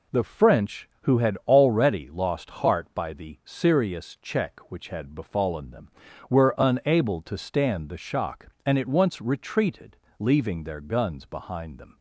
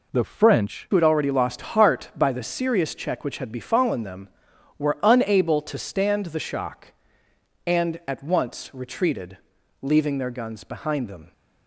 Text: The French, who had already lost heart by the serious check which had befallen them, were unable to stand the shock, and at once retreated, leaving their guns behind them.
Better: first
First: none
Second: changes voice at "who"; from 0.9 s on; 10.4 s long

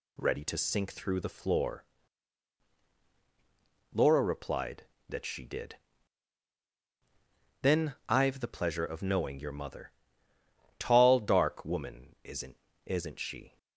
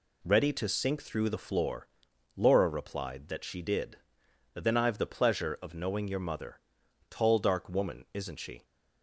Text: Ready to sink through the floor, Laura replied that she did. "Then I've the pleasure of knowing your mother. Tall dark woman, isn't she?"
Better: second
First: says "isn't" twice; at 12.8 s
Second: none

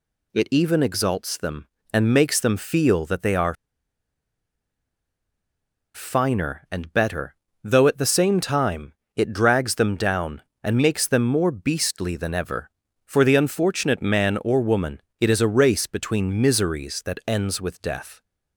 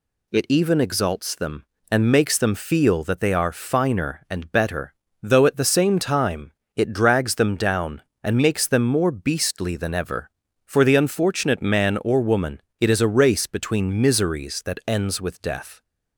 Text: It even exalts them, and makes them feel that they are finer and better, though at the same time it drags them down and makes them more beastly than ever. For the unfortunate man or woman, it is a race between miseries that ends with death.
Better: second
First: pauses between "are" and "finer"; strong; at 3.5 s; 2.4 s long // pauses between "time" and "it"; slight; at 8.9 s; 0.22 s long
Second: pauses between "time" and "it"; slight; at 6.5 s; 0.23 s long

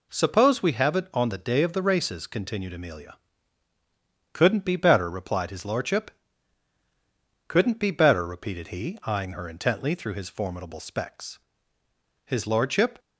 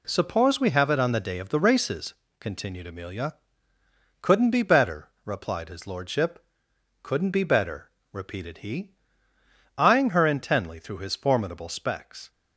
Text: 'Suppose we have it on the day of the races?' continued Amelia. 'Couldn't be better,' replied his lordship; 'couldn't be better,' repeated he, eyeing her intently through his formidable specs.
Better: second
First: goes on to say "His lordship"; noticeable; from 12.2 s on; 0.74 s long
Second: none

